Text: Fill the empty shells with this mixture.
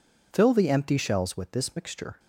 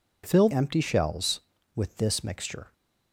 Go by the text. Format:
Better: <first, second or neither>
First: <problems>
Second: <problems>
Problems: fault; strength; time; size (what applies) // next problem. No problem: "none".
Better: first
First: none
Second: skips "the"; at 0.4 s